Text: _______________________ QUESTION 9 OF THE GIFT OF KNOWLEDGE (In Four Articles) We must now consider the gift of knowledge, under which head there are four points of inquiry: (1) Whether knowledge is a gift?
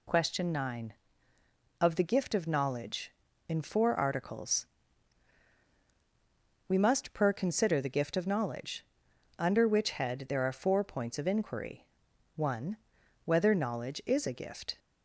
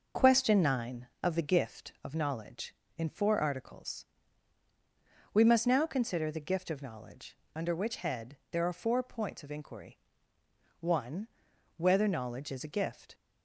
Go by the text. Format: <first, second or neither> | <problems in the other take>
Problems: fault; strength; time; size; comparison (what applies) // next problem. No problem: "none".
second | says "per" for "now"; at 7.1 s